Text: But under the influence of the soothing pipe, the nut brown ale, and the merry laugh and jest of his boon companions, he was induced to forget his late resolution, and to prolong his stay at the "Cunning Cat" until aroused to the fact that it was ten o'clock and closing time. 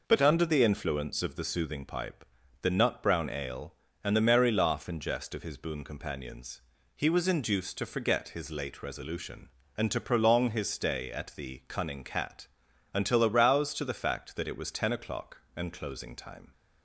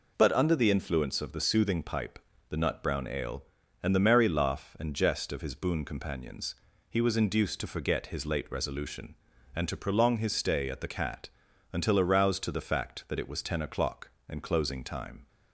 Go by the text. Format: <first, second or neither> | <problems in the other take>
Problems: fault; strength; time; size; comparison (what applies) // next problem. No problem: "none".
first | skips "Cunning"; at 10.8 s // pauses between "Cat" and "until"; at 11.2 s; 0.42 s long; noticeable in the first